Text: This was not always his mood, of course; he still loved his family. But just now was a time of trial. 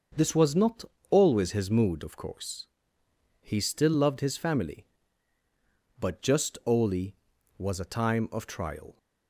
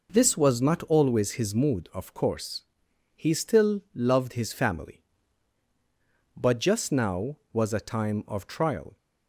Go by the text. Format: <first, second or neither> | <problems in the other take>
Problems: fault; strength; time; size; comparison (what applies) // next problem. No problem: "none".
second | starts louder than the rest; until 1.3 s; 6.5 dB // pauses between "not" and "always"; slight; at 0.8 s; 0.24 s long // says "oli" for "now"; at 6.6 s